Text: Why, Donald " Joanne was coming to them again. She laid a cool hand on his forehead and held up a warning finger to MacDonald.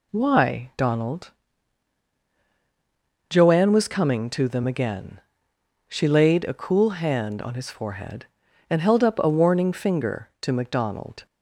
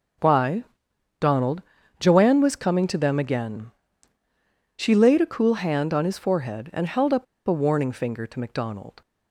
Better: first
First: none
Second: pauses between "up" and "a"; slight; at 7.2 s; 0.22 s long

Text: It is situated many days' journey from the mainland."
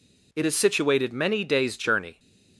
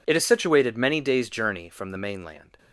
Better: second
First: stops before "from the mainland"; at 2.1 s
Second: none

